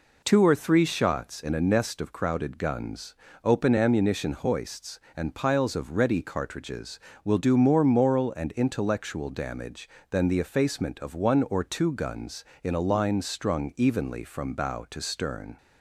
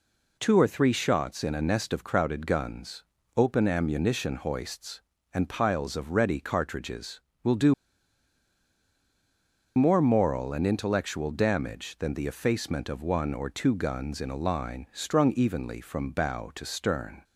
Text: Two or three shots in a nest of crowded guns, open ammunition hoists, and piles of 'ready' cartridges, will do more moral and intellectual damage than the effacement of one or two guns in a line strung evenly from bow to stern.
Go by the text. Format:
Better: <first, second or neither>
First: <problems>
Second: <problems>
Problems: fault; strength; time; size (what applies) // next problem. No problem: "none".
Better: first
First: none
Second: pauses between "do" and "more"; strong; at 7.7 s; 2.0 s long